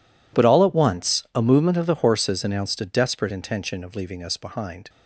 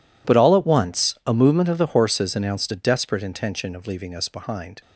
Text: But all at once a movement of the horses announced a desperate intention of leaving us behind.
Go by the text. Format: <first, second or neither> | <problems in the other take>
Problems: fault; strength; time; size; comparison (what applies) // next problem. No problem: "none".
neither | none